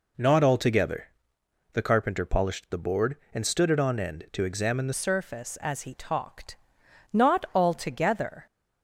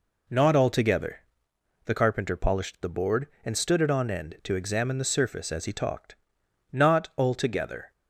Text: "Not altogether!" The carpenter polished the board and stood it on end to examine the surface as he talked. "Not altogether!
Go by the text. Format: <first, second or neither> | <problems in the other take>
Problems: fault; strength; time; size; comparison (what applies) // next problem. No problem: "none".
second | changes voice at "surface"; from 4.9 s on; 3.5 s long